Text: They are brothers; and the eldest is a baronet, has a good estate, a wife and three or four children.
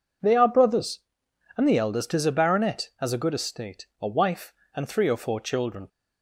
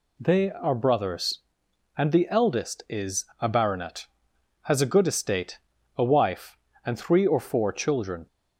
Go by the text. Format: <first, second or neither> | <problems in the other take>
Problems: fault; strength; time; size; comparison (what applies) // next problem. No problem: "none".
neither | none